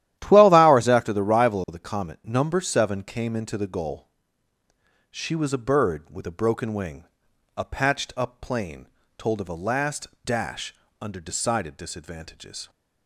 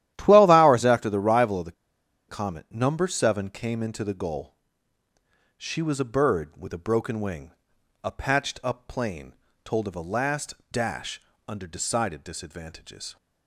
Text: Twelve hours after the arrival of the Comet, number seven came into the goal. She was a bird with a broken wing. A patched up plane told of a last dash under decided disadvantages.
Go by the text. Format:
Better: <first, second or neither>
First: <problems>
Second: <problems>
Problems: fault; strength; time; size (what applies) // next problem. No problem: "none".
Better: first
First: starts louder than the rest; strong; until 1.2 s; 12.5 dB // pauses between "plane" and "told"; slight; at 8.8 s; 0.32 s long // pauses between "last" and "dash"; slight; at 10.0 s; 0.16 s long // pauses between "dash" and "under"; slight; at 10.7 s; 0.28 s long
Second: starts louder than the rest; strong; until 1.1 s; 12.5 dB // pauses between "the" and "Comet"; noticeable; at 1.7 s; 0.56 s long // pauses between "plane" and "told"; slight; at 9.3 s; 0.32 s long // pauses between "last" and "dash"; slight; at 10.5 s; 0.16 s long // pauses between "dash" and "under"; slight; at 11.2 s; 0.28 s long